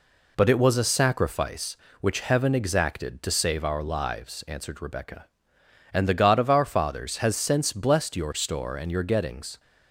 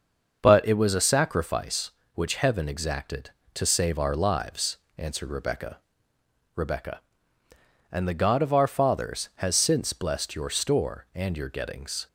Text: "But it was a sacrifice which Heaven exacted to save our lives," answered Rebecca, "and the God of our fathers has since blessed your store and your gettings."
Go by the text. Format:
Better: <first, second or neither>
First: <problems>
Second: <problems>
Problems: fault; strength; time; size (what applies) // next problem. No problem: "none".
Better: first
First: none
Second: starts louder than the rest; until 1.4 s; 6 dB // says "Rebecca" twice; at 6.5 s